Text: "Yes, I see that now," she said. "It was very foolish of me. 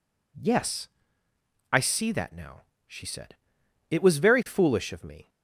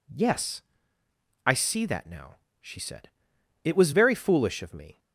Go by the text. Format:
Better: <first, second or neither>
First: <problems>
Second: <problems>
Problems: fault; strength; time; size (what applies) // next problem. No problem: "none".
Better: neither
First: none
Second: none